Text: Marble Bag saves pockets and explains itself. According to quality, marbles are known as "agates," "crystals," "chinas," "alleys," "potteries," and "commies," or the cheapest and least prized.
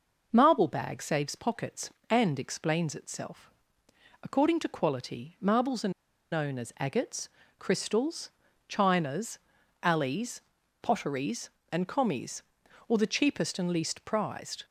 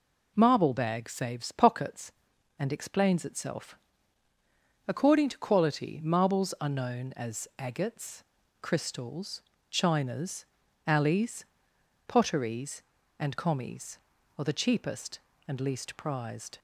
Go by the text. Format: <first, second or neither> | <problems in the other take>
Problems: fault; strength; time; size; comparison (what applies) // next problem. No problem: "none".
second | pauses between "are" and "known"; at 5.9 s; 0.40 s long